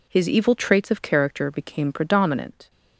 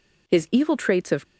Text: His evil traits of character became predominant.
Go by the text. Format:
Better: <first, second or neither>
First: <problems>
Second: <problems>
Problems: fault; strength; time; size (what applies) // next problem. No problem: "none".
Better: first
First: none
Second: stops before "character became predominant"; at 1.2 s